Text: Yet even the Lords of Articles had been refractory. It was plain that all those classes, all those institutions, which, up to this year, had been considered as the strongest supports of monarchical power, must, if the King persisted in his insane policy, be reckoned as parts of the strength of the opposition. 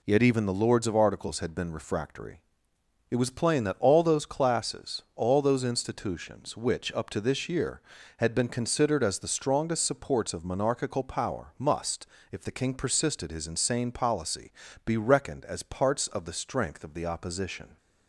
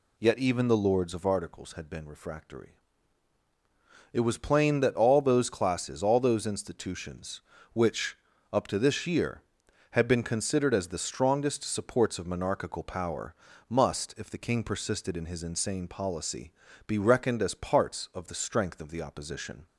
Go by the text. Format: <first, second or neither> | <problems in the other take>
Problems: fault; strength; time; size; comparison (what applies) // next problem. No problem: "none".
second | skips "in"; at 13.3 s